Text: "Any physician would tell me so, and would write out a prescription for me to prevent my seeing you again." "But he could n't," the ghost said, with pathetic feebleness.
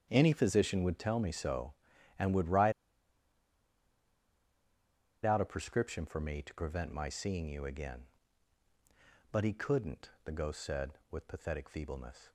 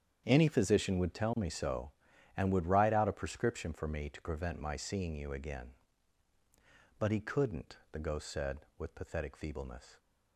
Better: second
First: starts louder than the rest; strong; until 1.1 s; 8 dB // pauses between "write" and "out"; strong; at 2.7 s; 2.5 s long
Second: starts louder than the rest; strong; until 1.2 s; 8 dB

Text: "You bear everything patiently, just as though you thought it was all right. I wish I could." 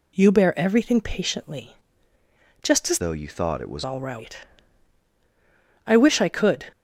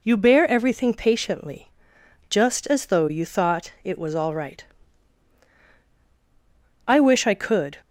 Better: second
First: changes voice from "though" to "was"; from 2.9 to 3.8 s; 0.9 s long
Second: none

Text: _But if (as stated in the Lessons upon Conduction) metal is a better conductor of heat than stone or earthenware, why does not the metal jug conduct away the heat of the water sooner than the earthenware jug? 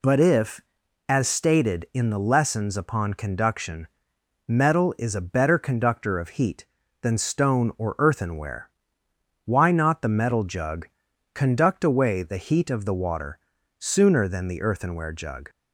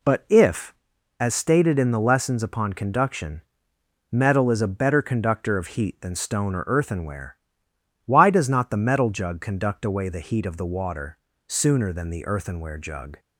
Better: second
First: skips "does"; at 9.7 s // pauses between "jug" and "conduct"; noticeable; at 10.8 s; 0.46 s long // pauses between "water" and "sooner"; at 13.3 s; 0.40 s long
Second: pauses between "water" and "sooner"; slight; at 11.1 s; 0.30 s long

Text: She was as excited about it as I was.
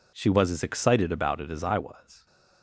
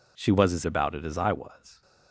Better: first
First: none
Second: skips "excited"; at 0.6 s

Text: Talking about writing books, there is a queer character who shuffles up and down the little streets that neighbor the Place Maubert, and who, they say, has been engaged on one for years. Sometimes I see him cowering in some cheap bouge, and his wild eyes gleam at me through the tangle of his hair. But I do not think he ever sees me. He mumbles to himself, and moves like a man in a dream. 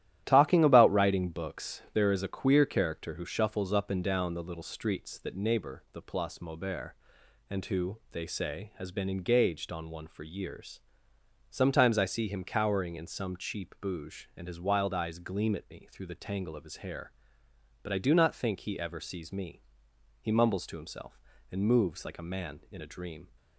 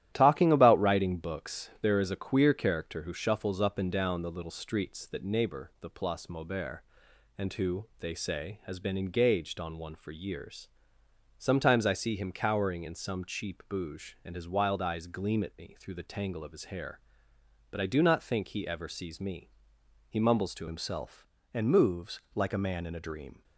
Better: first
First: starts louder than the rest; strong; until 1.2 s; 12.5 dB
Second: starts louder than the rest; strong; until 1.1 s; 12.5 dB // changes voice at "himself"; from 20.6 s on; 2.8 s long // pauses between "moves" and "like"; slight; at 22.1 s; 0.16 s long

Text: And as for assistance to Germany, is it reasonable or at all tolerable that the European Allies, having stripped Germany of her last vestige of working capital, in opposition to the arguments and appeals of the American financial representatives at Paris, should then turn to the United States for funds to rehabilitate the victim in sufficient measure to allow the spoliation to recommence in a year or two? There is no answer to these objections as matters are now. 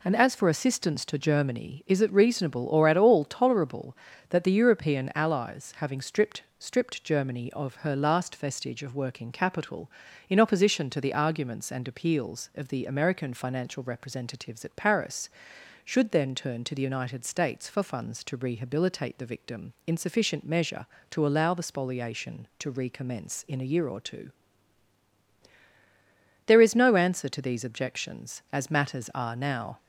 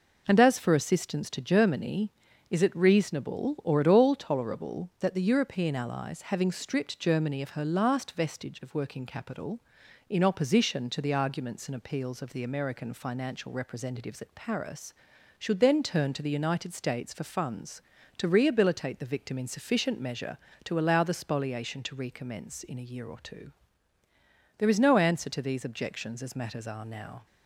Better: second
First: says "stripped" twice; at 6.5 s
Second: none

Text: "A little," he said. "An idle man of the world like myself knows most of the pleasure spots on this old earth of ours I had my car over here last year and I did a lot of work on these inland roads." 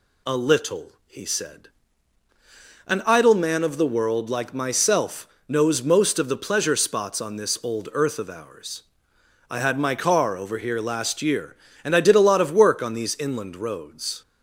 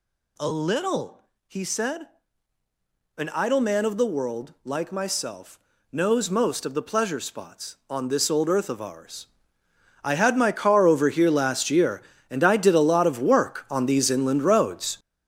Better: first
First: pauses between "myself" and "knows"; slight; at 5.2 s; 0.22 s long // pauses between "ours" and "I"; noticeable; at 8.8 s; 0.66 s long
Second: gets louder; strong; throughout; 8.5 dB // pauses between "myself" and "knows"; slight; at 5.5 s; 0.32 s long // pauses between "ours" and "I"; noticeable; at 9.2 s; 0.80 s long

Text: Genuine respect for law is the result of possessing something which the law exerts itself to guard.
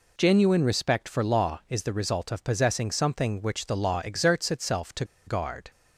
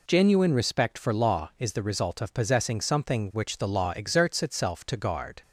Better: second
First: pauses between "to" and "guard"; slight; at 5.0 s; 0.22 s long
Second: none

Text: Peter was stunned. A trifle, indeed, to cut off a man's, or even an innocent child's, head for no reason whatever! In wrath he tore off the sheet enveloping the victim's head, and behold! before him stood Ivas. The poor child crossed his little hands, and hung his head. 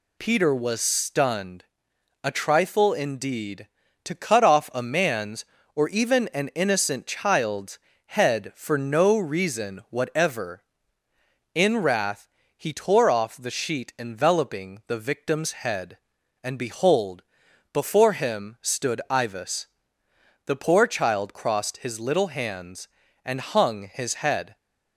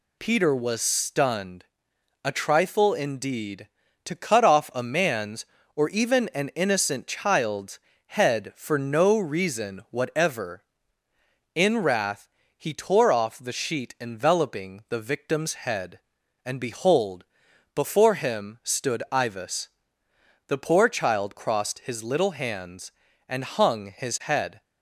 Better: neither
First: pauses between "wrath" and "he"; slight; at 12.2 s; 0.26 s long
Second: pauses between "wrath" and "he"; slight; at 12.2 s; 0.26 s long

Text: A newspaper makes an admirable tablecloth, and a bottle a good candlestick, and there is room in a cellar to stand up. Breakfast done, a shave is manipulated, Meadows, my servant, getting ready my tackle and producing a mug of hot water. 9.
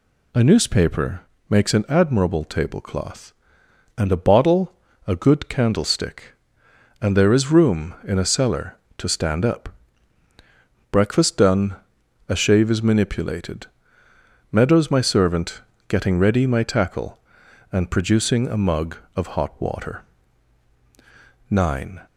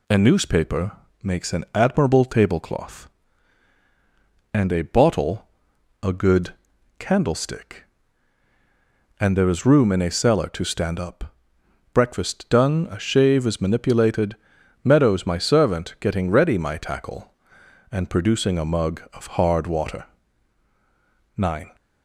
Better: first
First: pauses between "newspaper" and "makes"; slight; at 1.1 s; 0.30 s long // pauses between "bottle" and "a"; slight; at 4.7 s; 0.34 s long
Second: pauses between "newspaper" and "makes"; slight; at 0.9 s; 0.32 s long // pauses between "bottle" and "a"; noticeable; at 5.4 s; 0.56 s long // pauses between "good" and "candlestick"; noticeable; at 6.5 s; 0.46 s long // says "hard" for "hot"; at 19.2 s

